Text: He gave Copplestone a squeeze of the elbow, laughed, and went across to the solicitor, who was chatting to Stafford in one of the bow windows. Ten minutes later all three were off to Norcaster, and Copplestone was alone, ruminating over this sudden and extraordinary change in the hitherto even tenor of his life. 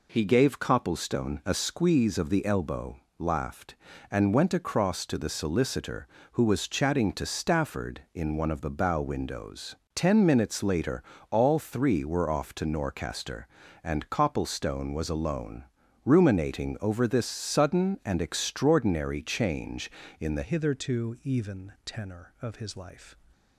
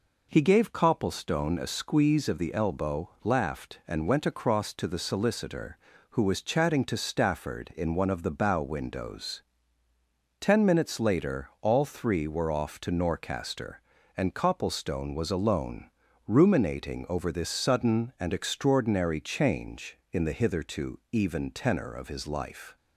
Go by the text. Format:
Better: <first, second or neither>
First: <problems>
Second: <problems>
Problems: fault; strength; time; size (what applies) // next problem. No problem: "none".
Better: second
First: pauses between "later" and "all"; slight; at 11.0 s; 0.30 s long // changes voice at "hitherto"; from 20.4 s on; 2.7 s long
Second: none